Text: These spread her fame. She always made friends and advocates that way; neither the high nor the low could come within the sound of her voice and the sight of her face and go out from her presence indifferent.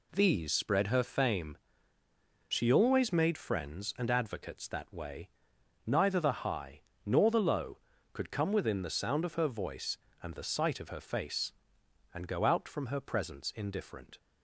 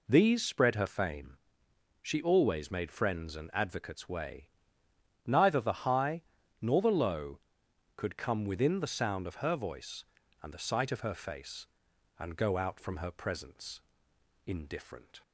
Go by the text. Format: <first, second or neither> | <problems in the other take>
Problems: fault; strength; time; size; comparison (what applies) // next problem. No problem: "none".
first | skips "that"; at 4.0 s // pauses between "high" and "nor"; slight; at 6.2 s; 0.36 s long; slight in the first // pauses between "presence" and "indifferent"; noticeable; at 13.7 s; 0.66 s long